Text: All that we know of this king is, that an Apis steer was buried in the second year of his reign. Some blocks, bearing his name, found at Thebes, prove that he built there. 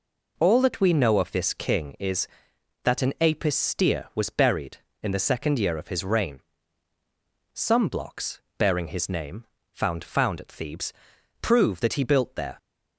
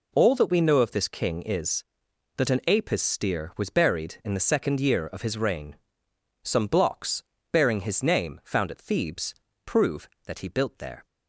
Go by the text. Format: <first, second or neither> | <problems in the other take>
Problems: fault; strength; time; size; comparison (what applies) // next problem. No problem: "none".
second | says "found" twice; at 10.0 s